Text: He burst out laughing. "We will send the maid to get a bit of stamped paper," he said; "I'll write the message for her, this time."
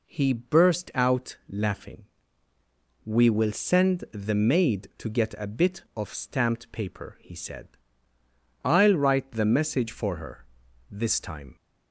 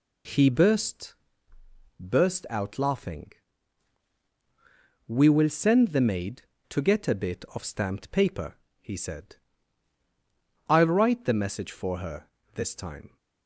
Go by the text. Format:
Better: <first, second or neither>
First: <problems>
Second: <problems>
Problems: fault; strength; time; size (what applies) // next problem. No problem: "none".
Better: first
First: none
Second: says "burst" twice; at 2.0 s